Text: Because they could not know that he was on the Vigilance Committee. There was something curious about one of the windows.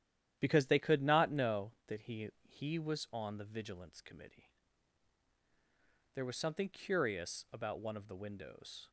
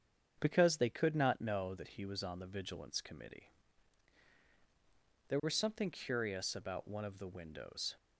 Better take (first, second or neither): second